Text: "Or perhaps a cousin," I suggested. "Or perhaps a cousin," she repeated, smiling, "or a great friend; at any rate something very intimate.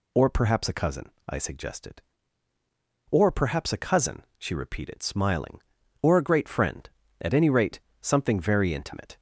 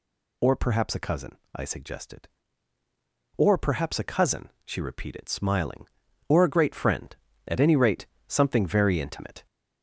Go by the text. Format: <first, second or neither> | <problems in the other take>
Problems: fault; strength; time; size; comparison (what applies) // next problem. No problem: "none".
first | gets louder; throughout; 4 dB // pauses between "rate" and "something"; slight; at 8.0 s; 0.22 s long; slight in the first